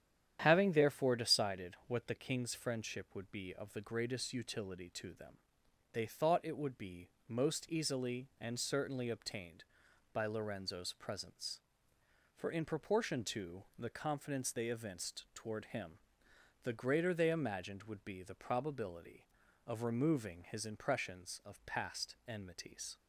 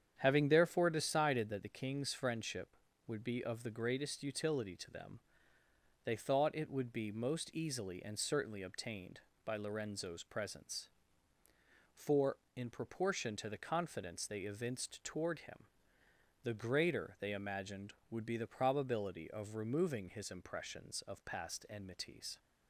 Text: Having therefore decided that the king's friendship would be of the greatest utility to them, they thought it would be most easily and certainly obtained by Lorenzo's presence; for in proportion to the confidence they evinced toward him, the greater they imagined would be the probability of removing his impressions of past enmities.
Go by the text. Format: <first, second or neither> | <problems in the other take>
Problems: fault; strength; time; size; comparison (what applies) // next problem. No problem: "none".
second | starts louder than the rest; strong; until 1.4 s; 10 dB; strong in the second // says "what" for "that"; at 1.8 s // pauses between "be" and "most"; slight; at 7.0 s; 0.20 s long